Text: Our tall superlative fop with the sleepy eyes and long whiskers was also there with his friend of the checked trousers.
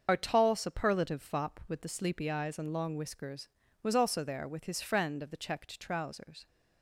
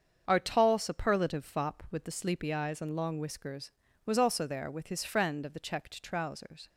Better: second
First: loses the start of "Our"; at 0.0 s; 40 ms // starts louder than the rest; until 1.0 s; 6.5 dB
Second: starts louder than the rest; until 1.2 s; 7 dB

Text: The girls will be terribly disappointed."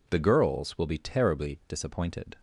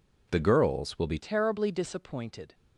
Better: first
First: none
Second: changes voice at "terribly"; from 1.1 s on; 1.4 s long

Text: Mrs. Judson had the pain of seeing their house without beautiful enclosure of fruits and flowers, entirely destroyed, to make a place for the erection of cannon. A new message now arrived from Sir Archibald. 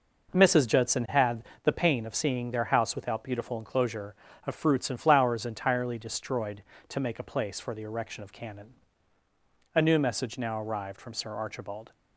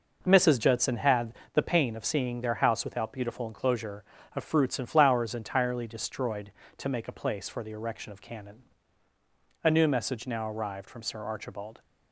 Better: neither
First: pauses between "had" and "the"; slight; at 1.4 s; 0.20 s long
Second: pauses between "had" and "the"; slight; at 1.3 s; 0.20 s long

